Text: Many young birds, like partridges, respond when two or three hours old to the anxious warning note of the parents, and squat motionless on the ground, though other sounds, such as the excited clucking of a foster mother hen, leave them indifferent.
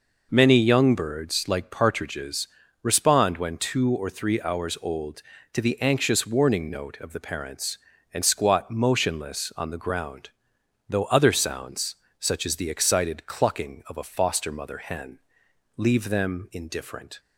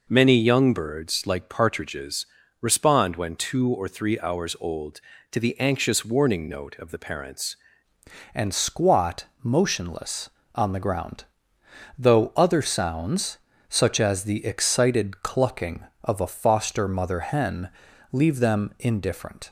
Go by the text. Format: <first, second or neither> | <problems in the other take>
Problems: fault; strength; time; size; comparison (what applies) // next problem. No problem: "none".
first | changes voice at "and"; from 8.3 s on; 11.1 s long // pauses between "squat" and "motionless"; slight; at 9.2 s; 0.18 s long